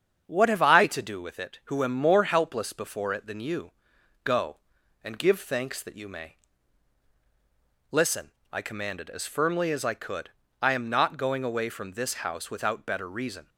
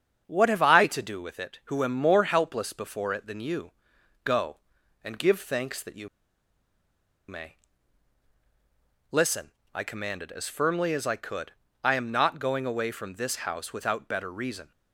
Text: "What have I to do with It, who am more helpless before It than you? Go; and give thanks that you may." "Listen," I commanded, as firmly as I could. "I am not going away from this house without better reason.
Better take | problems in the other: first | starts louder than the rest; strong; until 1.2 s; 7.5 dB; strong in the first // pauses between "you" and "may"; at 6.0 s; 1.2 s long

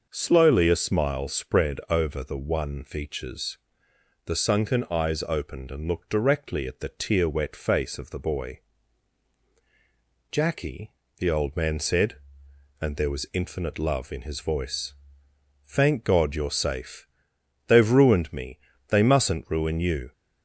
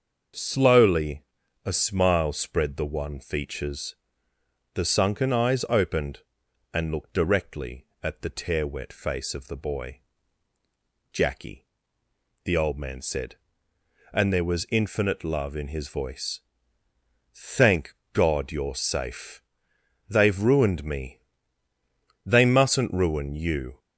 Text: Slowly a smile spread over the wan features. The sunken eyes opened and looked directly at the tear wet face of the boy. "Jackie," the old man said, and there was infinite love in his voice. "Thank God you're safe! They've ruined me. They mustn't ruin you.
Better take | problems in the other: first | starts louder than the rest; until 1.7 s; 6.5 dB // pauses between "Slowly" and "a"; at 1.2 s; 0.42 s long // skips "over"; at 2.7 s // pauses between "Thank" and "God"; slight; at 17.9 s; 0.18 s long

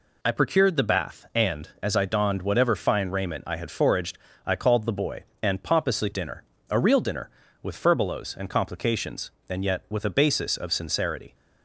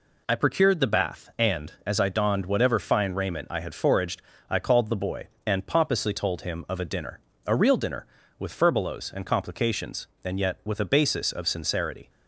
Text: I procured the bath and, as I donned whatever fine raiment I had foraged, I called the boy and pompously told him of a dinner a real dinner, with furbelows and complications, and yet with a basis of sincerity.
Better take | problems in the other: second | skips "told him of a"; at 6.1 s // pauses between "dinner" and "a"; slight; at 6.4 s; 0.28 s long; slight in the second

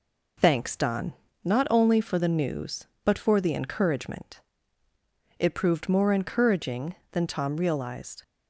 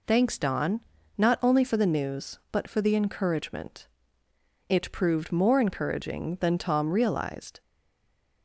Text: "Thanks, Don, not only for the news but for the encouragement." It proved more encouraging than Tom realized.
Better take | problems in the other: first | stays silent after the last word; slight; from 7.6 s on; 0.8 s long

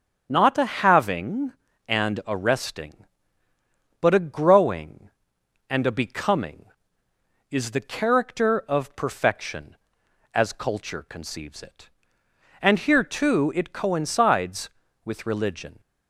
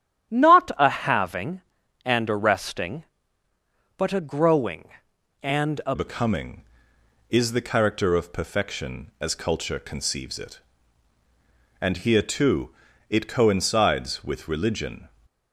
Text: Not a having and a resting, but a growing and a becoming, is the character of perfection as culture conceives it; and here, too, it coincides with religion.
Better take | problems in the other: first | starts louder than the rest; strong; until 1.3 s; 10.5 dB; strong in the first // changes voice at "becoming"; from 5.9 s on; 9.1 s long

